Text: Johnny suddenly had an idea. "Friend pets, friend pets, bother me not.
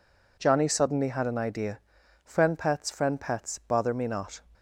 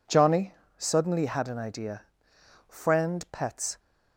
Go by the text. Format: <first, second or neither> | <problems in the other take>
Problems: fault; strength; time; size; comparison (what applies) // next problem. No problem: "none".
first | pauses between "Johnny" and "suddenly"; slight; at 0.5 s; 0.24 s long // stops before "friend pets bother me not"; at 3.7 s